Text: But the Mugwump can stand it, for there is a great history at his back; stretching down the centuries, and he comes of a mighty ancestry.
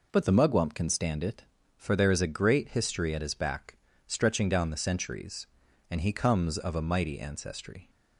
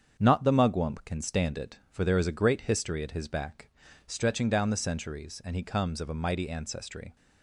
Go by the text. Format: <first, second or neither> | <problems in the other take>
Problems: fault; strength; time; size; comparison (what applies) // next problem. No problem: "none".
first | starts louder than the rest; strong; until 1.2 s; 7.5 dB // says "Not" for "But"; at 0.1 s